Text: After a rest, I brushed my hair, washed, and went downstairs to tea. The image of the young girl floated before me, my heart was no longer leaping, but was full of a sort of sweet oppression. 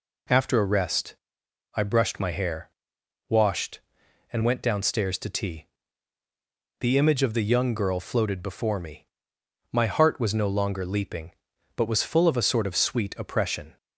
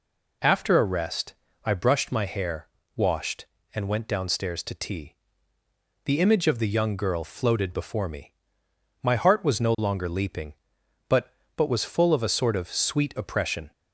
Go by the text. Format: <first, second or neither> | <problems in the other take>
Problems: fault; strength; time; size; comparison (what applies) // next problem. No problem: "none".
first | says "but" twice; at 11.5 s